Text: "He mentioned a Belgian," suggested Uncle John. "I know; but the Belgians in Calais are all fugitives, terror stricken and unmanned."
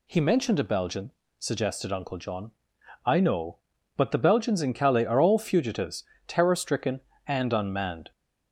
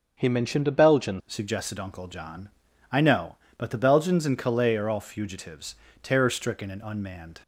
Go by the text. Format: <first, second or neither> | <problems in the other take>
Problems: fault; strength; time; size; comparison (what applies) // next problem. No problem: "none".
first | changes voice at "suggested"; from 1.2 s on; 6.2 s long